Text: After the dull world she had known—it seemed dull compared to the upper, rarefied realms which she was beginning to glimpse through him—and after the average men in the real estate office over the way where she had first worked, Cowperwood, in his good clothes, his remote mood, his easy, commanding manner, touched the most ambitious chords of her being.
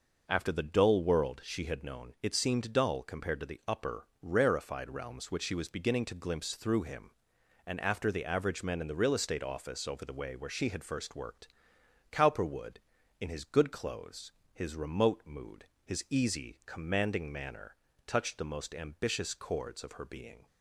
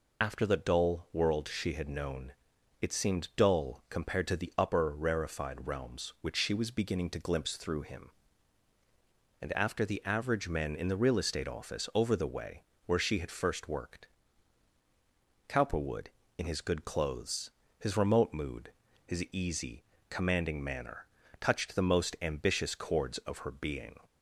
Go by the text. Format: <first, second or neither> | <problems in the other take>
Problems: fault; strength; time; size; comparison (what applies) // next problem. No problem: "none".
first | loses the start of "After"; at 0.2 s; 100 ms // pauses between "way" and "where"; slight; at 12.6 s; 0.20 s long